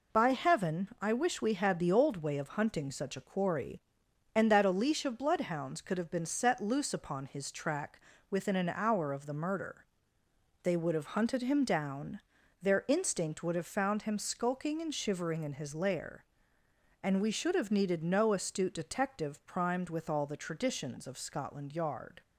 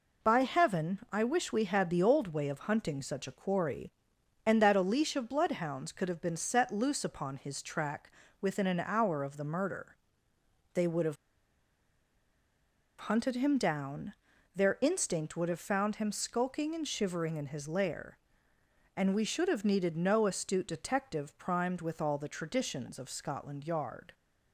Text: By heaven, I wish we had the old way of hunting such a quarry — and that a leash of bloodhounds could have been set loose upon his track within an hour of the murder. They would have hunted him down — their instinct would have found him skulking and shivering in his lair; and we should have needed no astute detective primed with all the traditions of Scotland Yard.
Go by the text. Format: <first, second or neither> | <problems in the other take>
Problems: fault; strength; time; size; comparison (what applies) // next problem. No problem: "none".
first | pauses between "track" and "within"; slight; at 8.1 s; 0.30 s long; slight in the first // pauses between "have" and "hunted"; strong; at 11.1 s; 1.8 s long